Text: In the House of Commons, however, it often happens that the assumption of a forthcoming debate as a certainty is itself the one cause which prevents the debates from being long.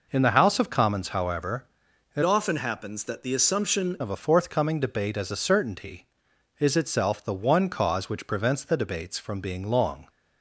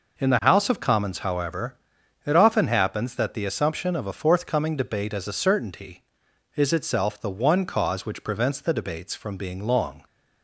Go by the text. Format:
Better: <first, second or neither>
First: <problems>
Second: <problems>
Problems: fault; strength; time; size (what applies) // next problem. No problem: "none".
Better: second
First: changes voice from "often" to "assumption"; from 2.2 to 3.9 s; 1.7 s long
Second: none